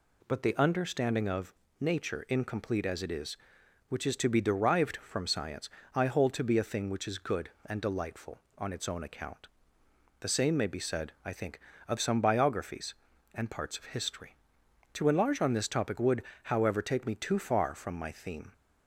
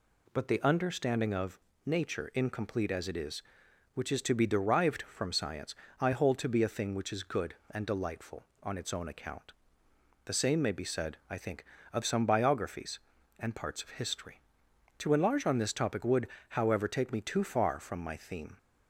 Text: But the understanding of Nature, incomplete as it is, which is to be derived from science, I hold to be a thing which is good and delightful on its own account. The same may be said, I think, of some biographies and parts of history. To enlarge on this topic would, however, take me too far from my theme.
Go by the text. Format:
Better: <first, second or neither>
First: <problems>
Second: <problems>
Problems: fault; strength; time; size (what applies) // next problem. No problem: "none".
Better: neither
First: pauses between "of" and "Nature"; slight; at 1.5 s; 0.26 s long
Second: pauses between "of" and "Nature"; slight; at 1.5 s; 0.26 s long